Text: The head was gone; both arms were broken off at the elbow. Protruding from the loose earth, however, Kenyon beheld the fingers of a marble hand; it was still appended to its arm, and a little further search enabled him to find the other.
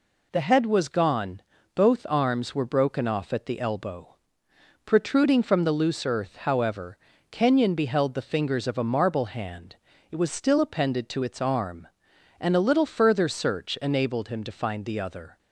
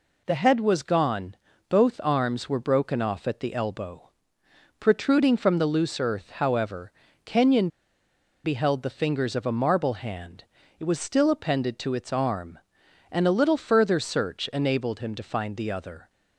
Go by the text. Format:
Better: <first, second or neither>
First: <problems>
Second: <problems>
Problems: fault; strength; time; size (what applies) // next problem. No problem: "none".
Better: first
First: none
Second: pauses between "Kenyon" and "beheld"; noticeable; at 7.6 s; 0.77 s long